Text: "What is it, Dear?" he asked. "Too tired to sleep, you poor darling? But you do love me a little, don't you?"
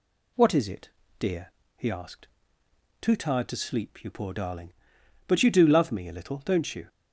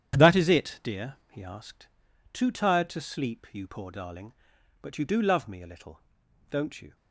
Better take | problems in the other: first | starts louder than the rest; strong; until 1.3 s; 9.5 dB // says "That" for "What"; at 0.1 s

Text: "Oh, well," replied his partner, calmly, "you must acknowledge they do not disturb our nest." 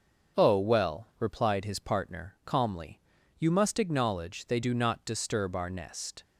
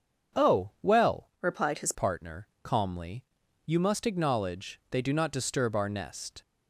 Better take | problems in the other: first | starts louder than the rest; until 1.5 s; 7 dB; also in the first // changes voice from "replied" to "his"; from 1.4 to 1.9 s; 0.5 s long

